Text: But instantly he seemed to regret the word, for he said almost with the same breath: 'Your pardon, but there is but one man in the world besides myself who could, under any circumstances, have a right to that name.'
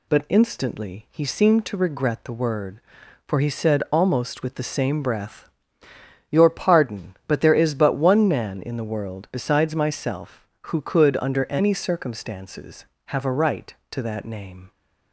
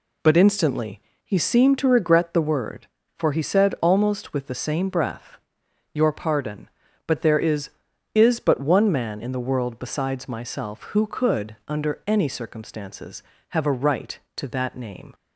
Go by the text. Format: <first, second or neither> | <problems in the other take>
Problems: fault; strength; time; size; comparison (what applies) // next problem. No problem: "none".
first | pauses between "instantly" and "he"; slight; at 1.0 s; 0.24 s long // says "is" twice; at 8.1 s